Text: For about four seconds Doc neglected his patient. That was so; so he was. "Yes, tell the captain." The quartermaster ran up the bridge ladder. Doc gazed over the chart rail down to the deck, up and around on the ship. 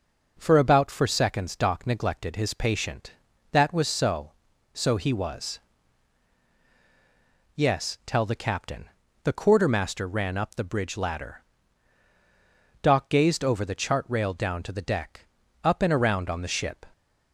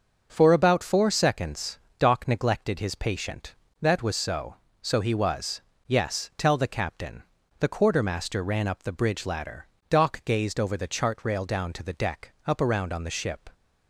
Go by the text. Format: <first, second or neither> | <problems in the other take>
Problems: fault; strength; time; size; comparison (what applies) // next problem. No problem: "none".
first | starts louder than the rest; until 1.3 s; 6.5 dB // pauses between "seconds" and "Doc"; slight; at 1.7 s; 0.22 s long // skips "and"; at 12.6 s